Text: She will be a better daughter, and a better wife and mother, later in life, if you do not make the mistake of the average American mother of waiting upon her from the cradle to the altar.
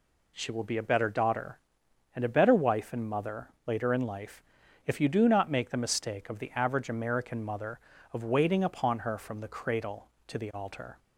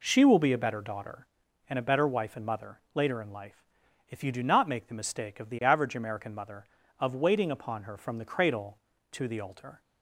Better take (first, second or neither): neither